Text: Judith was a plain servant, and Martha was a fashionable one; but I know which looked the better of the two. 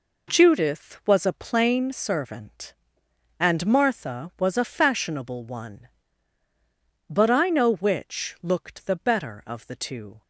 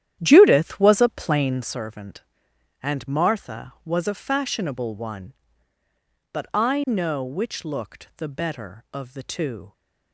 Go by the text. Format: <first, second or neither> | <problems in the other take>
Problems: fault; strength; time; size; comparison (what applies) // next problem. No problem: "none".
first | starts louder than the rest; strong; until 1.8 s; 11 dB